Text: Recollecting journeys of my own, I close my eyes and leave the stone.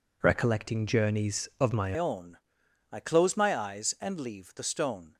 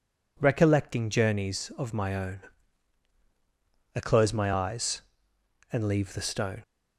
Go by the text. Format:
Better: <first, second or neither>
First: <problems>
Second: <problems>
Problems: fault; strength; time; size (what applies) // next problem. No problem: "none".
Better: second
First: changes voice at "own"; from 1.9 s on; 3.2 s long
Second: none